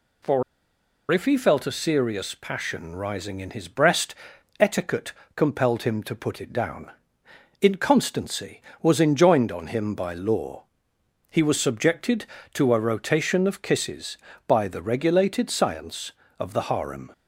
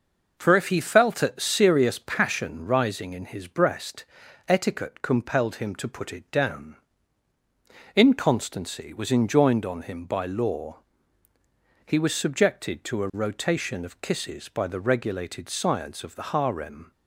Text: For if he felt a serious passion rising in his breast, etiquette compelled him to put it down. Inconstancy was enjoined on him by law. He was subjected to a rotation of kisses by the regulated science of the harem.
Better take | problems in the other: second | pauses between "For" and "if"; noticeable; at 0.4 s; 0.68 s long // pauses between "etiquette" and "compelled"; slight; at 5.1 s; 0.24 s long

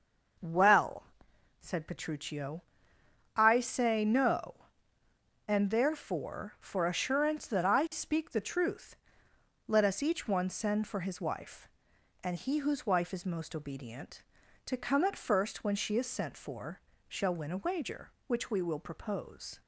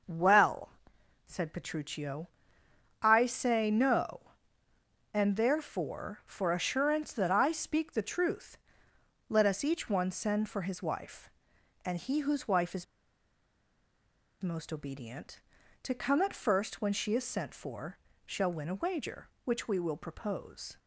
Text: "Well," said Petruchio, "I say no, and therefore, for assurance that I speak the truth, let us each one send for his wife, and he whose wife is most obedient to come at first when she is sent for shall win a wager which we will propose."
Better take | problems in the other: first | pauses between "is" and "most"; strong; at 12.8 s; 1.5 s long // pauses between "for" and "shall"; slight; at 17.9 s; 0.26 s long; slight in the first

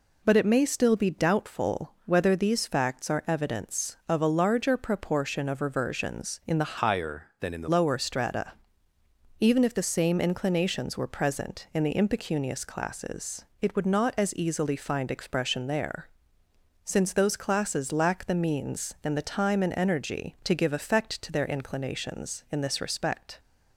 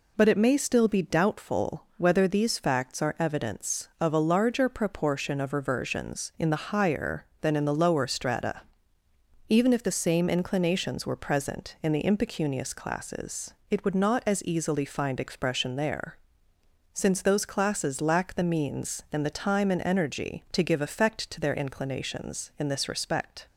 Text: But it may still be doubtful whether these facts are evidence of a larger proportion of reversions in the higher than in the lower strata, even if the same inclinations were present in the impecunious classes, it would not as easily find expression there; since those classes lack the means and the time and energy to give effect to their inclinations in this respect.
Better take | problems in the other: second | changes voice from "higher" to "the"; from 6.7 to 7.6 s; 0.9 s long

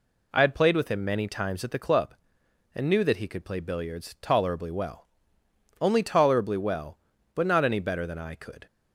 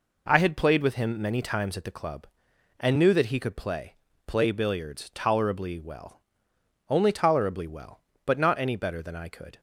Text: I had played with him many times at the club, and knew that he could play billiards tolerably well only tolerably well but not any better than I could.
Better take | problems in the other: first | says "play" twice; at 4.2 s // pauses between "well" and "only"; noticeable; at 6.1 s; 0.70 s long; noticeable in the first

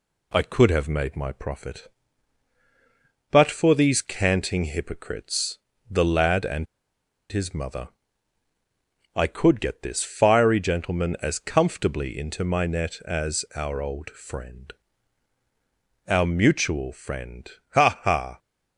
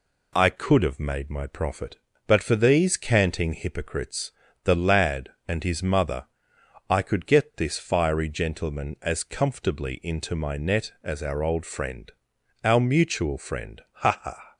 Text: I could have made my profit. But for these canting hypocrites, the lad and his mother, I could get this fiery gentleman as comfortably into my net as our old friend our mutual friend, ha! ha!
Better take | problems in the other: second | pauses between "and" and "his"; noticeable; at 6.6 s; 0.66 s long // pauses between "friend" and "our"; strong; at 14.7 s; 1.3 s long; noticeable in the second

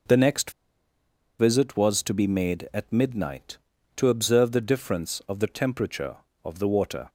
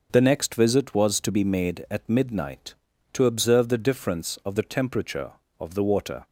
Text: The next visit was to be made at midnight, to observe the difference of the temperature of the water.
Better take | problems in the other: second | pauses between "next" and "visit"; noticeable; at 0.5 s; 0.88 s long

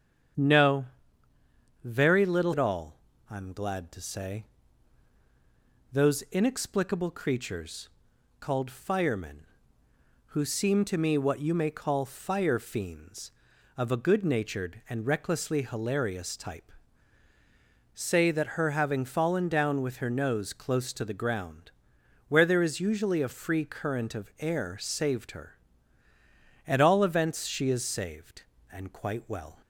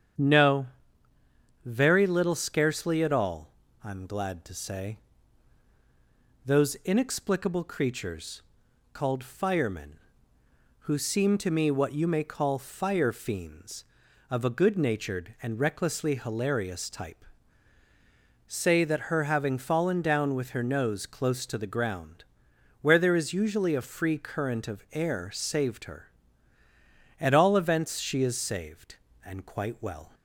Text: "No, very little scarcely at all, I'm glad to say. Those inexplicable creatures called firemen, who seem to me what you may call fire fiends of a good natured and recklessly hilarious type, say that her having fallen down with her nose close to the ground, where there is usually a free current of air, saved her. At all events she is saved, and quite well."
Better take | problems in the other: second | starts louder than the rest; strong; until 2.3 s; 8 dB; strong in the second // skips "scarcely"; at 2.5 s // pauses between "creatures" and "called"; noticeable; at 7.8 s; 0.52 s long; noticeable in the second

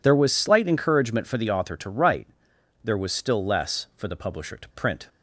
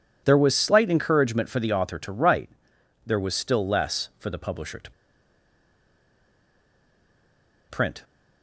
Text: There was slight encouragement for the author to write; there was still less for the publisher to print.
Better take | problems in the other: first | pauses between "to" and "print"; strong; at 4.8 s; 2.8 s long

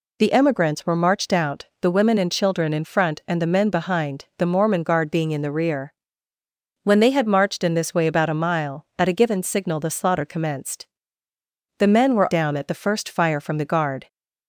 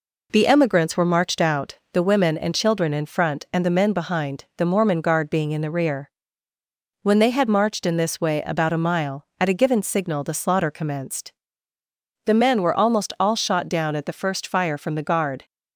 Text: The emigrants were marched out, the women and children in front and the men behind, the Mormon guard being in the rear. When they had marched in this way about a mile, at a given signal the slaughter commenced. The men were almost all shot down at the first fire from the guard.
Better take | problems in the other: second | skips "almost all shot"; at 12.3 s

